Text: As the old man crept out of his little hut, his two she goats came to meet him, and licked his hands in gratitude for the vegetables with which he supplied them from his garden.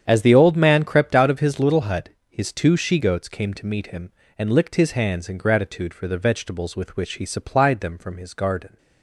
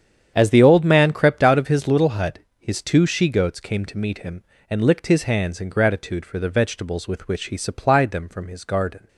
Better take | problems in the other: neither | starts louder than the rest; strong; the same in both

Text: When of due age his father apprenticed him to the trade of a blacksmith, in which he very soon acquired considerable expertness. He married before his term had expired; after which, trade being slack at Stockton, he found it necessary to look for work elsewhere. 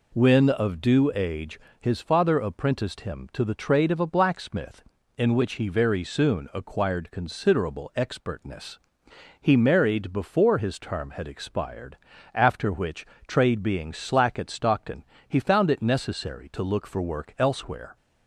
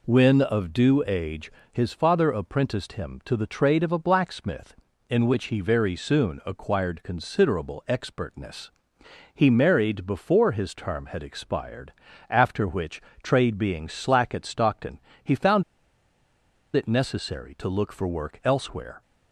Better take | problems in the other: first | pauses between "age" and "his"; slight; at 1.5 s; 0.22 s long; slight in the first // pauses between "found" and "it"; at 15.6 s; 1.1 s long

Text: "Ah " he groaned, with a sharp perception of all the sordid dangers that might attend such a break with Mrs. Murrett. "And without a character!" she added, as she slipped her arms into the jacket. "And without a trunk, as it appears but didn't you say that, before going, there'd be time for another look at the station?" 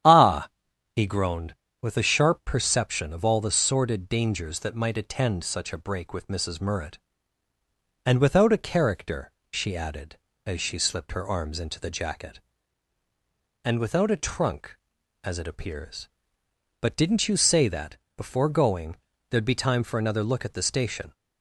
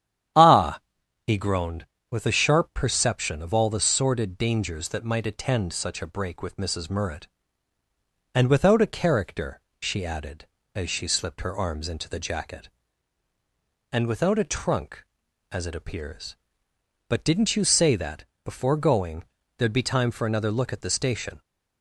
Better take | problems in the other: neither | starts louder than the rest; strong; the same in both

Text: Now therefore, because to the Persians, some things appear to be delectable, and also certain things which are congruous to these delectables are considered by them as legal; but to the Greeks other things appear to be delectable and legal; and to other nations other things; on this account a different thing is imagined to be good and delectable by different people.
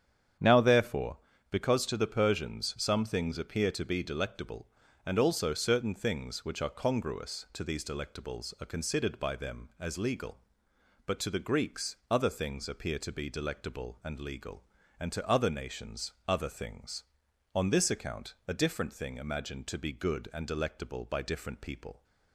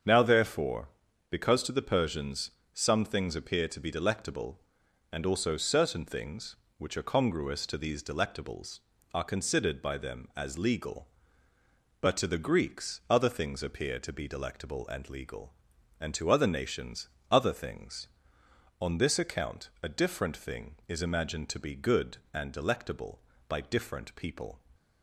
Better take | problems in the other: second | starts louder than the rest; strong; until 1.7 s; 8.5 dB; also in the second // pauses between "nations" and "other"; slight; at 16.1 s; 0.16 s long; slight in the second // skips "is"; at 19.1 s

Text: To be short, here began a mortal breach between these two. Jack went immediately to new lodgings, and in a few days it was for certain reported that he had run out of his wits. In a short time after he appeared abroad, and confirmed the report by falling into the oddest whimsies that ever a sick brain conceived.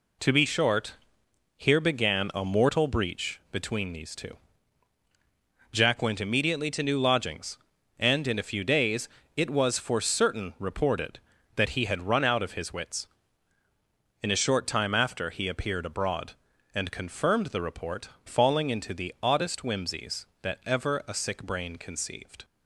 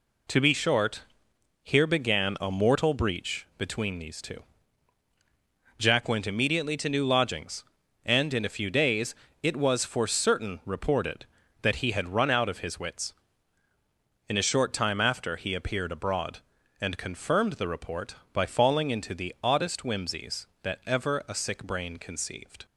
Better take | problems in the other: second | pauses between "days" and "it"; slight; at 9.0 s; 0.28 s long; slight in the second // skips "by"; at 18.1 s

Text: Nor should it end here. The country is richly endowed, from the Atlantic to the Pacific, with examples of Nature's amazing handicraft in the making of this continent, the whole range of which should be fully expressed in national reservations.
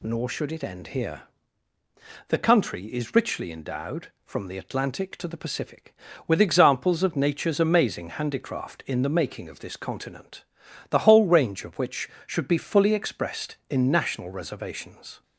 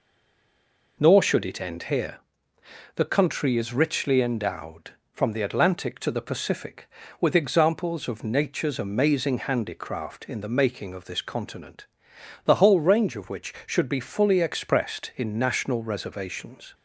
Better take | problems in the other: first | stays silent before the first word; until 0.9 s; 0.9 s long

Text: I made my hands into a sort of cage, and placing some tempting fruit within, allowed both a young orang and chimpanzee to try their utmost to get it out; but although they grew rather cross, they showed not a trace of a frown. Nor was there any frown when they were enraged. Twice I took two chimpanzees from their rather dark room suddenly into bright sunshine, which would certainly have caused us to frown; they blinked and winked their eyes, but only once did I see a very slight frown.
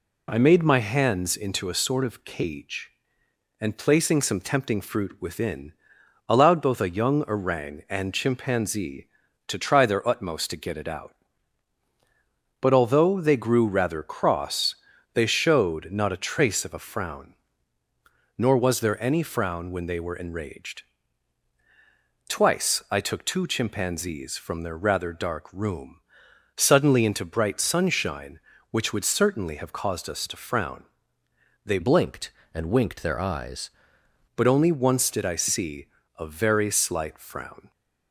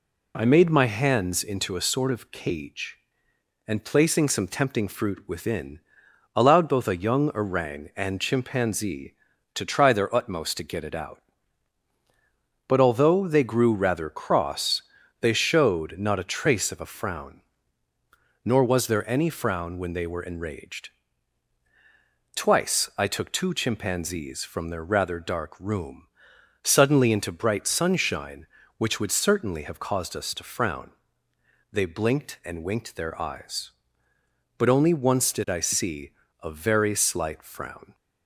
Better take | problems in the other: second | pauses between "room" and "suddenly"; noticeable; at 26.0 s; 0.54 s long; noticeable in the second // changes voice from "blinked" to "eyes"; from 31.8 to 33.7 s; 1.9 s long // pauses between "see" and "a"; slight; at 35.8 s; 0.30 s long; slight in the second

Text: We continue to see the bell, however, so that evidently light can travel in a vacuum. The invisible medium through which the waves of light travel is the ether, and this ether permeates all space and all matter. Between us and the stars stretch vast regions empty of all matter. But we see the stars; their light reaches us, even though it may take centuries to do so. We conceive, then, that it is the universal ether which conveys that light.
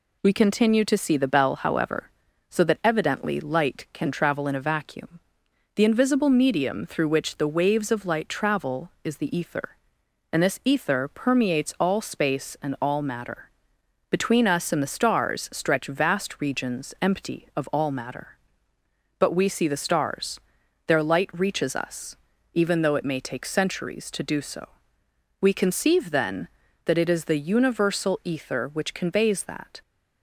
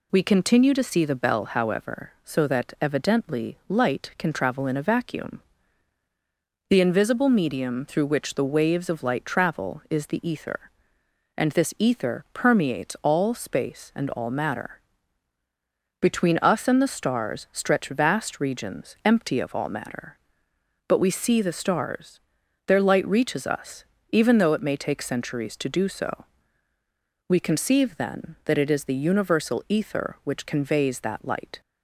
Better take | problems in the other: second | stops before "light"; at 29.8 s

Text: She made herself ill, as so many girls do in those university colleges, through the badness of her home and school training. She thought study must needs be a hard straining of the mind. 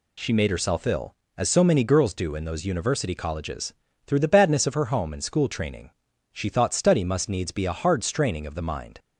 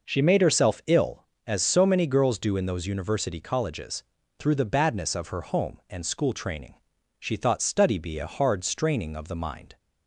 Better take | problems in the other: first | skips "must needs"; at 7.9 s

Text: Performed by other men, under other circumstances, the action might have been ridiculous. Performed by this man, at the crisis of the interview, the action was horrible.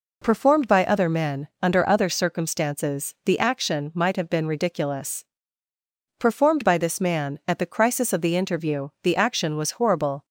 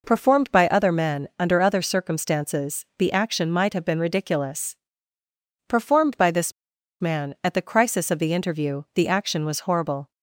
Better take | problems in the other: first | pauses between "this" and "man"; noticeable; at 6.5 s; 0.48 s long

